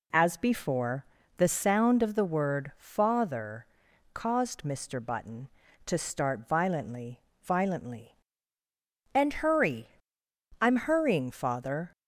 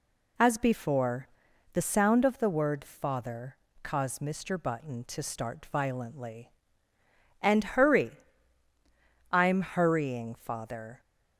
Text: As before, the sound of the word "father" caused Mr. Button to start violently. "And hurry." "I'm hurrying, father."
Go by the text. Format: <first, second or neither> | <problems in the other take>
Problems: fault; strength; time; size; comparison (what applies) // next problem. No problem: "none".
second | pauses between "father" and "caused"; noticeable; at 3.6 s; 0.48 s long; slight in the second // says "violently" twice; at 7.4 s